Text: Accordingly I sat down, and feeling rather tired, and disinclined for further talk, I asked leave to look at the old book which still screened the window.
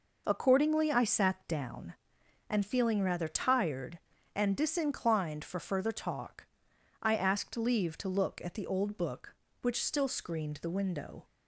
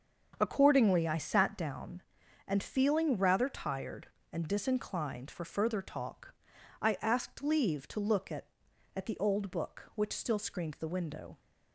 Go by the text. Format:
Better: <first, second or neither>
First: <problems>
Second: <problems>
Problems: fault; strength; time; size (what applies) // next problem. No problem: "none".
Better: first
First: none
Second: starts louder than the rest; strong; until 1.4 s; 7 dB // says "at" twice; at 8.9 s